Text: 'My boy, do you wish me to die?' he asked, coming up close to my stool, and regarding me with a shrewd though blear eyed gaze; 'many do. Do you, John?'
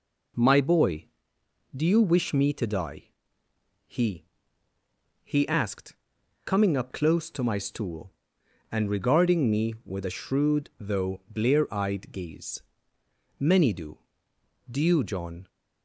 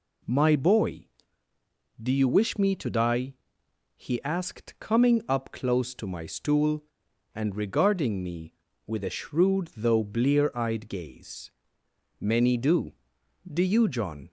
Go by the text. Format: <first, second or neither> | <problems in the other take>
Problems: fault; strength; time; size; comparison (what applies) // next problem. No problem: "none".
second | says "he" twice; at 5.2 s